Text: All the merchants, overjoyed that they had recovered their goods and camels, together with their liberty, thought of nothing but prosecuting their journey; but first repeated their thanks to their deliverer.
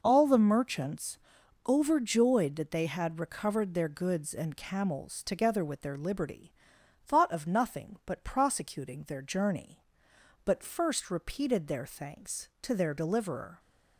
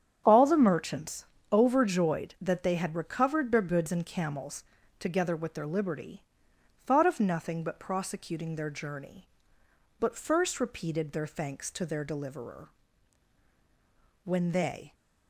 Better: first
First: none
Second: starts louder than the rest; strong; until 1.2 s; 9 dB // goes on to say "When they"; noticeable; from 14.2 s on; 0.70 s long

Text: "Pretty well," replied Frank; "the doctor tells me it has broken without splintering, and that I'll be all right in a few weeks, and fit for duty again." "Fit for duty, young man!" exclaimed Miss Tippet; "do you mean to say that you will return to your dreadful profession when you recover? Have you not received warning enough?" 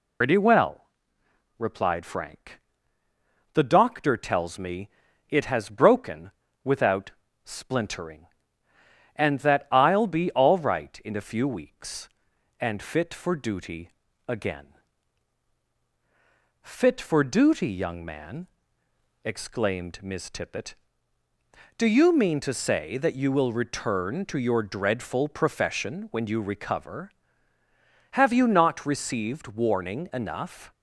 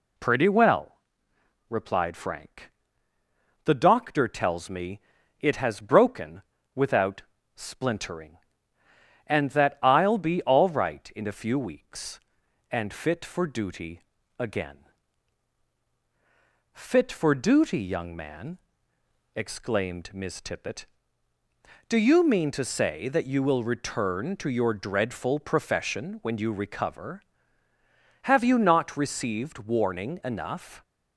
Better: second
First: loses the start of "Pretty"; at 0.2 s; 130 ms // pauses between "me" and "it"; at 4.8 s; 0.40 s long // pauses between "broken" and "without"; slight; at 6.3 s; 0.32 s long // pauses between "without" and "splintering"; slight; at 7.1 s; 0.32 s long // pauses between "duty" and "again"; at 13.8 s; 0.38 s long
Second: pauses between "me" and "it"; at 5.0 s; 0.40 s long // pauses between "broken" and "without"; slight; at 6.4 s; 0.32 s long // pauses between "without" and "splintering"; slight; at 7.2 s; 0.32 s long // pauses between "duty" and "again"; at 14.0 s; 0.38 s long

